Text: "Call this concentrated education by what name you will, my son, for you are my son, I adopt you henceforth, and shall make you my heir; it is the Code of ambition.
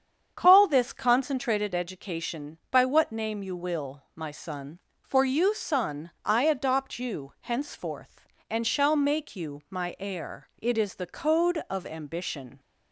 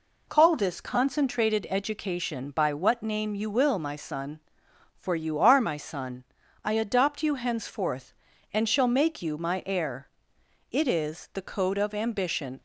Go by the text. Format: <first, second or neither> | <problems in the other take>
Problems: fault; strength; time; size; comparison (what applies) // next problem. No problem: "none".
second | starts louder than the rest; strong; until 1.3 s; 8 dB // skips "are my"; at 5.5 s